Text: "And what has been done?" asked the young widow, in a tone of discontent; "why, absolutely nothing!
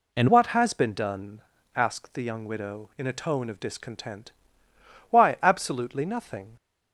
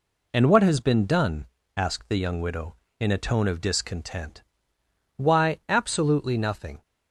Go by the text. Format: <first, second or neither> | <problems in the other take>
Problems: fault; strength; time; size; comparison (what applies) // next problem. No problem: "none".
second | changes voice at "what"; from 0.2 s on; 6.3 s long